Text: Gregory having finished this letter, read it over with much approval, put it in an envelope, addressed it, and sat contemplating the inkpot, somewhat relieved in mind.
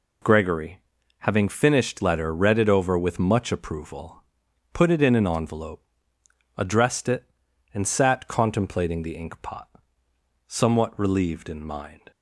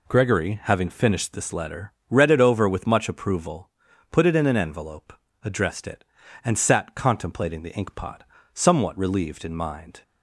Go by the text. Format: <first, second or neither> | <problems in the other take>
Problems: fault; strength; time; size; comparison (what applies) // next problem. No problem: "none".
second | pauses between "Gregory" and "having"; at 0.7 s; 0.40 s long // skips "this"; at 2.0 s